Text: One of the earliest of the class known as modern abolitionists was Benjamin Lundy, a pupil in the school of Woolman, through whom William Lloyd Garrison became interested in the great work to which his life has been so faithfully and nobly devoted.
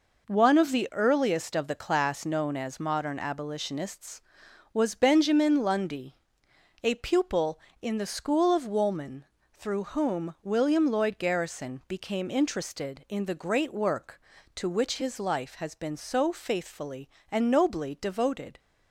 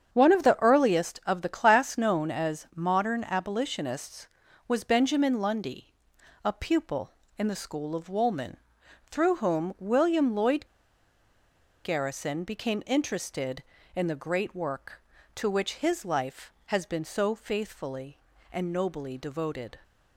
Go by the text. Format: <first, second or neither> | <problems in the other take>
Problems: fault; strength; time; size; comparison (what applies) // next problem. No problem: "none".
first | starts louder than the rest; strong; until 1.1 s; 8 dB // pauses between "Lloyd" and "Garrison"; at 10.6 s; 1.1 s long